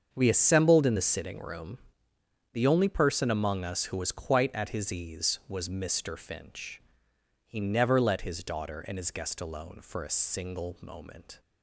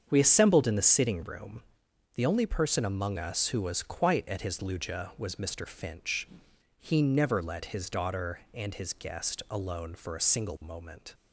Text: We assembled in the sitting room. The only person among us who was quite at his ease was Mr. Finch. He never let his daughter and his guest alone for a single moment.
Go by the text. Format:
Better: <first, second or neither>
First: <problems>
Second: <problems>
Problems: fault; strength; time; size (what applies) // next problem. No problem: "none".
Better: first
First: starts louder than the rest; until 1.1 s; 7 dB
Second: starts louder than the rest; strong; until 1.1 s; 7.5 dB // says "luja" for "ease"; at 4.5 s